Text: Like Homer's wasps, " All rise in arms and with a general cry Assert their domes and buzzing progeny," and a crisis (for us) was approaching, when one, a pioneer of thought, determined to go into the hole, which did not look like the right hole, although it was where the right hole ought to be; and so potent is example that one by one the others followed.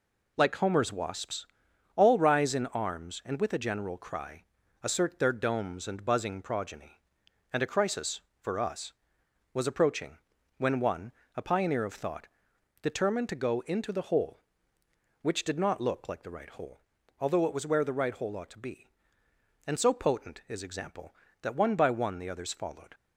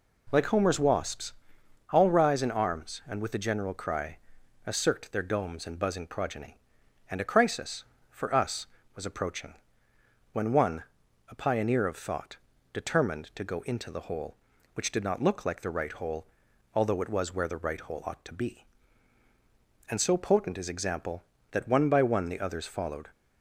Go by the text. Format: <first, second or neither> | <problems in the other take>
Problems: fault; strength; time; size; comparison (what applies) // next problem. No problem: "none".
neither | pauses between "cry" and "Assert"; the same in both